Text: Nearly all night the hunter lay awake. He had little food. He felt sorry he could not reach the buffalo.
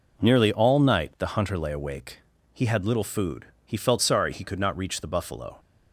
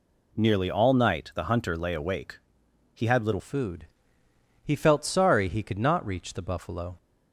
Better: first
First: none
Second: changes voice at "food"; from 3.3 s on; 3.6 s long

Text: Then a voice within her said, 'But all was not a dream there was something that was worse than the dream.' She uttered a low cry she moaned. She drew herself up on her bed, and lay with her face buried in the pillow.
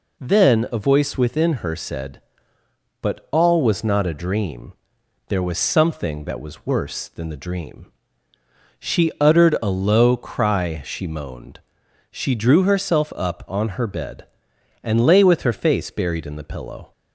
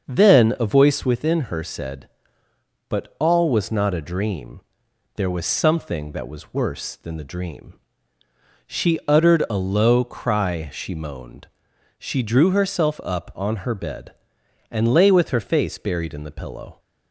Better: first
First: pauses between "dream" and "there"; noticeable; at 4.7 s; 0.56 s long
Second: starts louder than the rest; until 1.1 s; 6.5 dB // pauses between "dream" and "there"; noticeable; at 4.6 s; 0.56 s long

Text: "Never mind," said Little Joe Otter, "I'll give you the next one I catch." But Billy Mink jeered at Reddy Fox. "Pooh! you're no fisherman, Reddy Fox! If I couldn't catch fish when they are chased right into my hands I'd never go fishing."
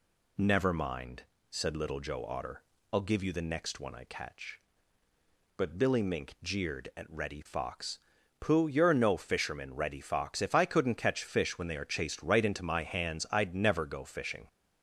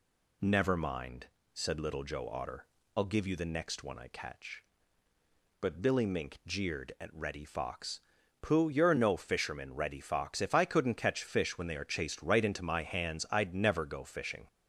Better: neither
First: none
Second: none

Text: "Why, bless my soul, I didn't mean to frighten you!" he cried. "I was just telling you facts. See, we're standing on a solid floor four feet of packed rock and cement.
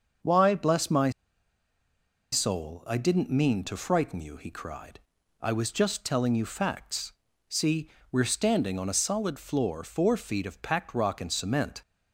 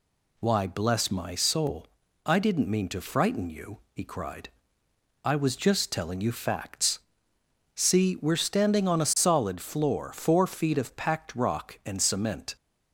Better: second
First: starts louder than the rest; until 2.4 s; 6.5 dB // pauses between "my" and "soul"; at 1.0 s; 1.2 s long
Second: none

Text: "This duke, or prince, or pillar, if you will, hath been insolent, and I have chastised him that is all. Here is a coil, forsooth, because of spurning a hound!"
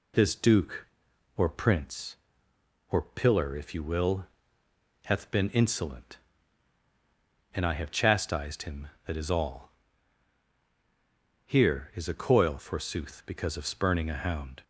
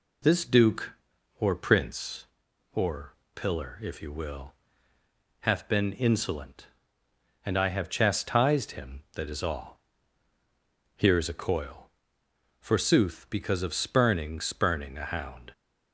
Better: first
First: none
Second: pauses between "or" and "pillar"; slight; at 3.1 s; 0.22 s long // says "spurning" twice; at 14.3 s

